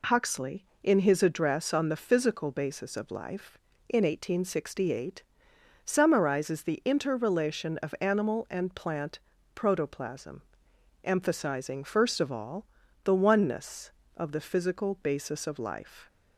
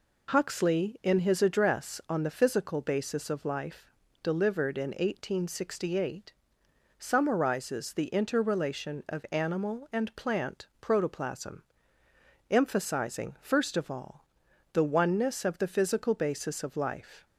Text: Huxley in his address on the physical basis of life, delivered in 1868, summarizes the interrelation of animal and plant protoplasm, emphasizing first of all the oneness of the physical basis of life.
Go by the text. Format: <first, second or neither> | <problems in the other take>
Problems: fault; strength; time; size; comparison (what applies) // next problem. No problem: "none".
second | skips "delivered"; at 3.7 s // pauses between "plant" and "protoplasm"; slight; at 9.1 s; 0.36 s long // pauses between "all" and "the"; at 12.6 s; 0.40 s long; noticeable in the second